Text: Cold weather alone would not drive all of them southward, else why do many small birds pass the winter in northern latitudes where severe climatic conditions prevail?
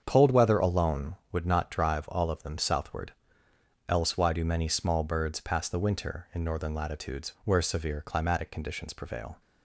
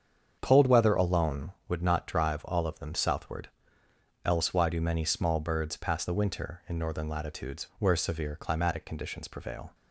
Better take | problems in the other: neither | starts louder than the rest; strong; the same in both

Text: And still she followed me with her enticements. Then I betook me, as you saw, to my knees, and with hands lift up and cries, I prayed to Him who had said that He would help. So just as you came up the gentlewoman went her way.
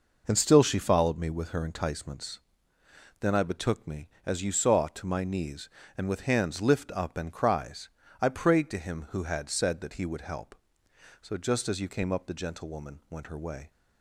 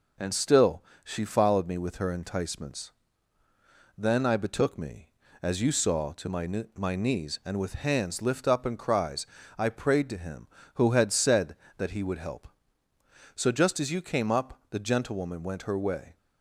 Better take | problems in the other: first | pauses between "still" and "she"; slight; at 0.8 s; 0.20 s long // says "my" twice; at 6.7 s

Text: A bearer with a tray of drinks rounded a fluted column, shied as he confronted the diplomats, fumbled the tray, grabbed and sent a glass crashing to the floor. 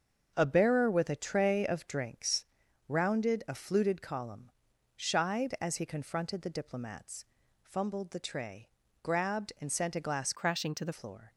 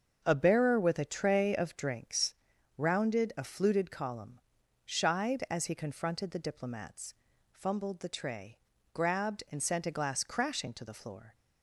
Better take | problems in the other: second | starts louder than the rest; until 1.3 s; 6.5 dB; also in the second // pauses between "drinks" and "rounded"; at 2.4 s; 0.44 s long; also in the second // changes voice from "crashing" to "the"; from 10.3 to 10.9 s; 0.6 s long

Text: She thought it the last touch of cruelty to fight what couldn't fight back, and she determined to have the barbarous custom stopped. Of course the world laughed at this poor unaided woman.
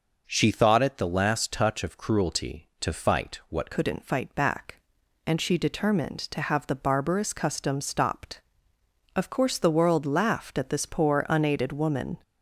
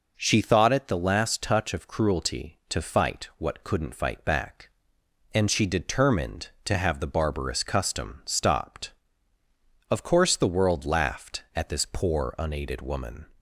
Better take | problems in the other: second | changes voice at "couldn't"; from 3.7 s on; 8.4 s long

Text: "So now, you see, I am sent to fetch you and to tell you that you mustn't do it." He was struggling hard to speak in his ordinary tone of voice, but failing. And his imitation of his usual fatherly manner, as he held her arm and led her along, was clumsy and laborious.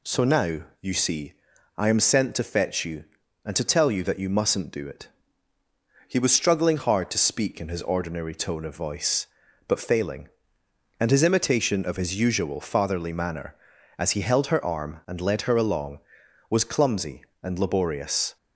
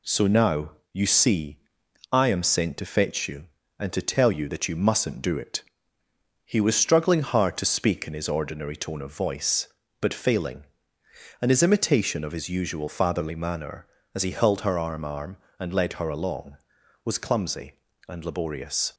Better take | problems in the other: first | says "arm" twice; at 15.0 s

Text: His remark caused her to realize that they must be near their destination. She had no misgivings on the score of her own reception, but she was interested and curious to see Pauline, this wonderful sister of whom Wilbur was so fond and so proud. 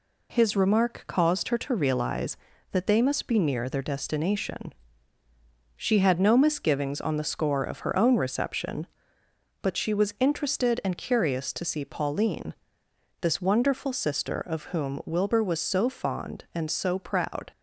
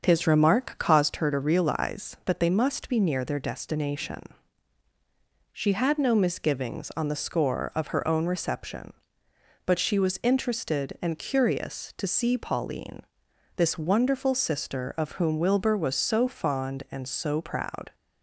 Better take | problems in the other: first | starts louder than the rest; until 1.1 s; 6.5 dB

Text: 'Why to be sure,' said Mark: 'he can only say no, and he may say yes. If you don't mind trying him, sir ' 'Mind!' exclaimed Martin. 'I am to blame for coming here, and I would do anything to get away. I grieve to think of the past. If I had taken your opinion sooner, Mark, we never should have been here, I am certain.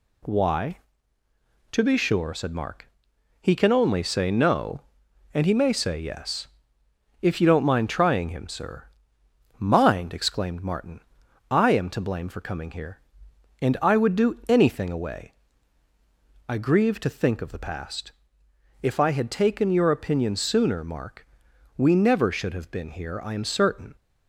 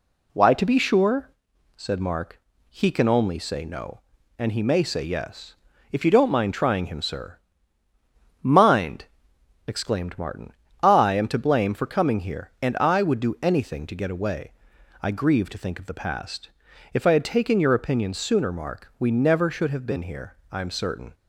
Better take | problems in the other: second | skips "to get"; at 14.8 s

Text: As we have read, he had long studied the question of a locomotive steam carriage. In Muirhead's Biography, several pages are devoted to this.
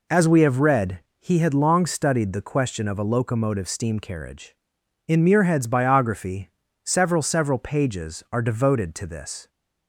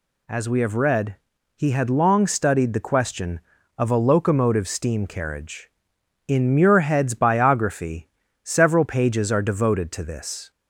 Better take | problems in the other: second | says "several" twice; at 7.2 s

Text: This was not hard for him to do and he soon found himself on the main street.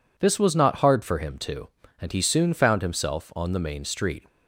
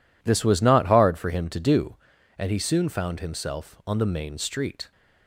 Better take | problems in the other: second | skips "do"; at 1.8 s

